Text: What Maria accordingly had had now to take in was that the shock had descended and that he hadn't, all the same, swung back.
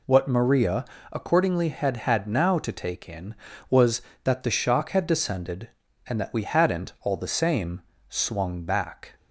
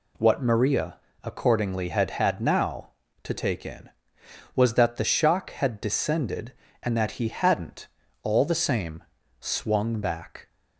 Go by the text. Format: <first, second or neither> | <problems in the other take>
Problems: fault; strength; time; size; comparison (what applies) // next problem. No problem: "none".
second | pauses between "Maria" and "accordingly"; slight; at 0.8 s; 0.26 s long; slight in the second // says "we" for "he"; at 6.3 s